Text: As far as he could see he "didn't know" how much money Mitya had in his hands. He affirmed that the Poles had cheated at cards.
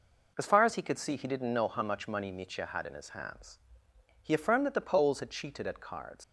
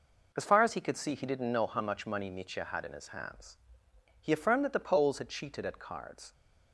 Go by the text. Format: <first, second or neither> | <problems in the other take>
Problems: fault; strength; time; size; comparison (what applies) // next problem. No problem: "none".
second | leaves "cards" unfinished; at 6.2 s; 95 ms